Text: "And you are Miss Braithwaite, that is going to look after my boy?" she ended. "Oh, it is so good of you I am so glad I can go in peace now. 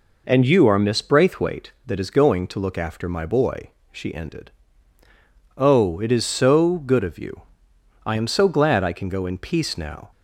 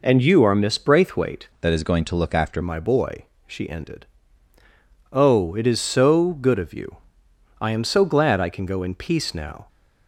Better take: first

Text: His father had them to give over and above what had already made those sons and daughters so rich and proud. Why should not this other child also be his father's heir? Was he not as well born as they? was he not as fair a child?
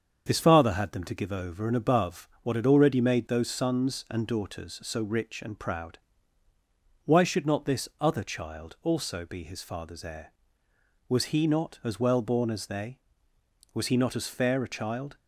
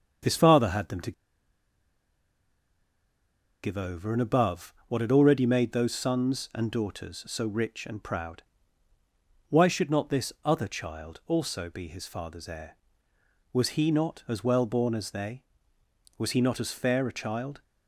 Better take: first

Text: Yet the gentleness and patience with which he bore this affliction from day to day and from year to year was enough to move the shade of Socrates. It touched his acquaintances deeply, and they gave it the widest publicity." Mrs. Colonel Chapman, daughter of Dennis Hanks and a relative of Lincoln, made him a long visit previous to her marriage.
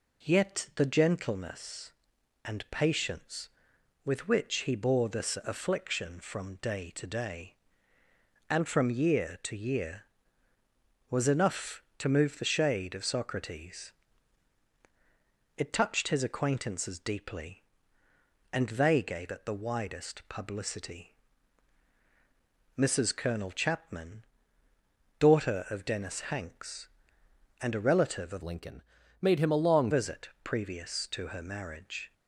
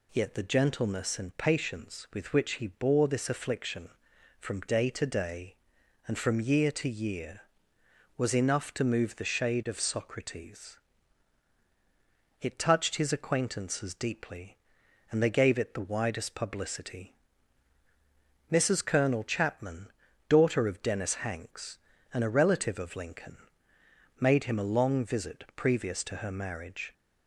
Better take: second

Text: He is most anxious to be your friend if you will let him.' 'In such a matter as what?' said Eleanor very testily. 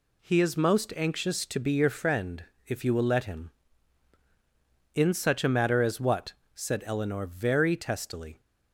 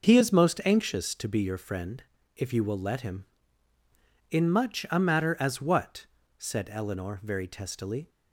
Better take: first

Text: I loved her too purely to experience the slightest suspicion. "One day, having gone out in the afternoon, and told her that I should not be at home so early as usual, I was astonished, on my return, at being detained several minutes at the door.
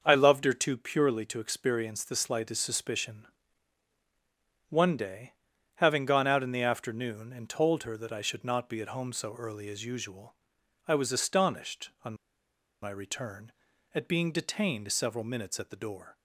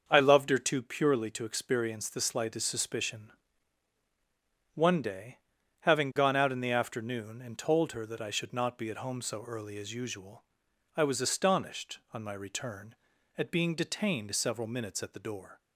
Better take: second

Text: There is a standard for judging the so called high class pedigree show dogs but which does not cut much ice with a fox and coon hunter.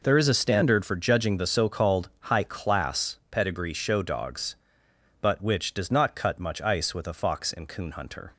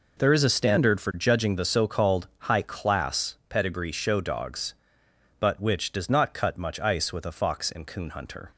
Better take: neither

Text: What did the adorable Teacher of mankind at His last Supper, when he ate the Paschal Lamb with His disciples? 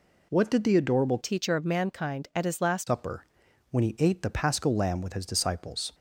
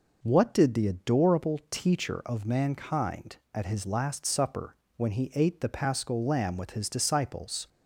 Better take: second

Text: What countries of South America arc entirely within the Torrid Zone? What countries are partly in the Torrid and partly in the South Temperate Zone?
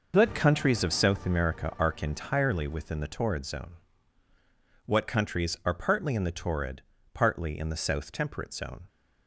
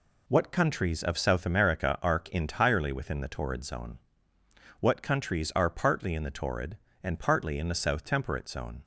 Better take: second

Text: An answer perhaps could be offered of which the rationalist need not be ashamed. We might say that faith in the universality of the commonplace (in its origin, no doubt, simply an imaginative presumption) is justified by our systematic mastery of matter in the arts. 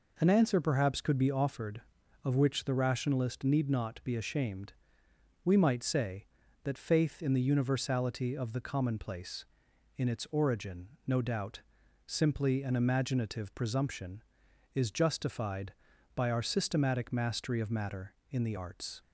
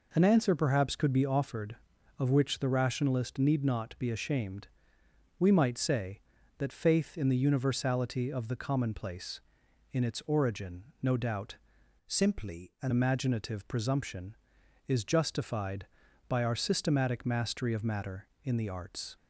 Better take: first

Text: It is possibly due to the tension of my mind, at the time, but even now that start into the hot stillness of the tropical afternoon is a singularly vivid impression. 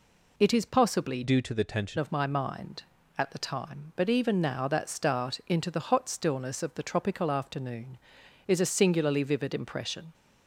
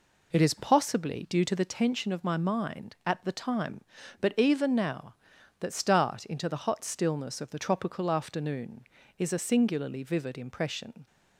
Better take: second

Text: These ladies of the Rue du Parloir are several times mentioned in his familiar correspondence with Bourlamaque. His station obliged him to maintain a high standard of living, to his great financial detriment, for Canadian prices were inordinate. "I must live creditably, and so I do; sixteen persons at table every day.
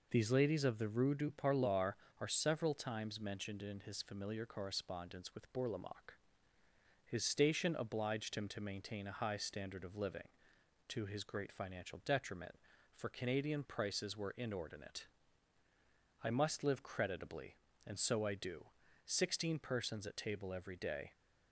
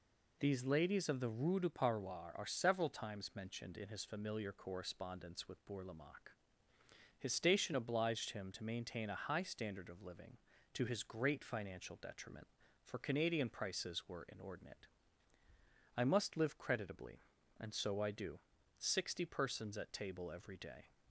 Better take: first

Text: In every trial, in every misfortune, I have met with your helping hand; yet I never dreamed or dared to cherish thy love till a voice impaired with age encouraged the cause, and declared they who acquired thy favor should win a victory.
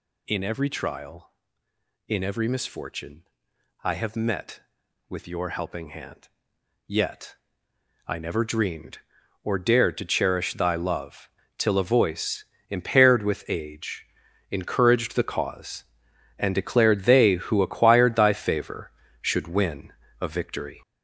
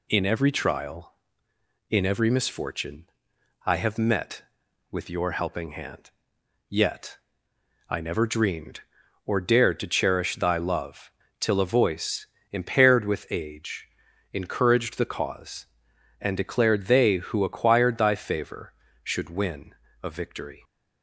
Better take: second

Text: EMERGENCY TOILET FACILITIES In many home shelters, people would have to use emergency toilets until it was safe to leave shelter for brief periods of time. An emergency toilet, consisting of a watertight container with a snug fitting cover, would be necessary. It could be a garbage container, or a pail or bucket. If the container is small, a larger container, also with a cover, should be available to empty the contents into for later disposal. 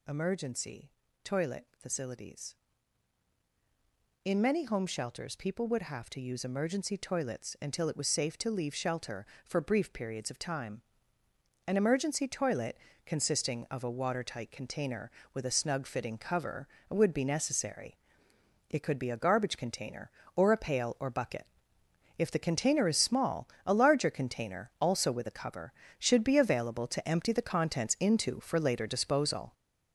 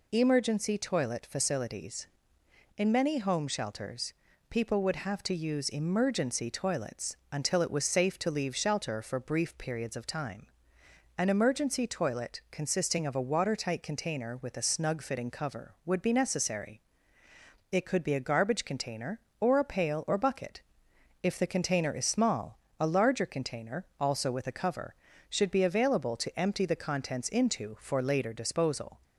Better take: second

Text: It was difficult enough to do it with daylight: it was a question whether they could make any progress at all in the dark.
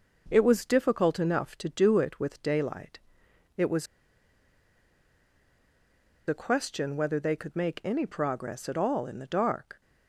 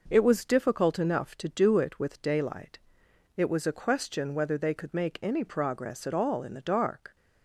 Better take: second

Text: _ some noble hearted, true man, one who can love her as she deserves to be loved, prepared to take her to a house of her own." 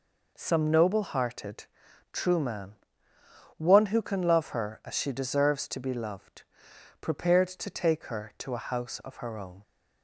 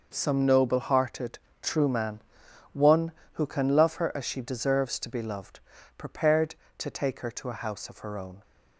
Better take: neither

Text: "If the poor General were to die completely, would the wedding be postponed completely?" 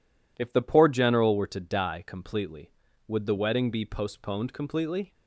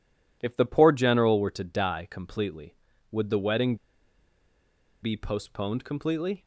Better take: first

